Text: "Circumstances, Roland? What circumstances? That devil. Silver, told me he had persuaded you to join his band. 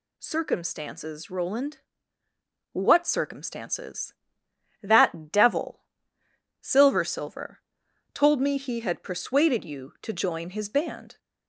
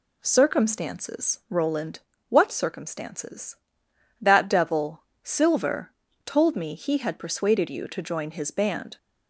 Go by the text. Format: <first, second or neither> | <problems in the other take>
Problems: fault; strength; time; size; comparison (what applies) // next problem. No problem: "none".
second | says "Silver" twice; at 7.0 s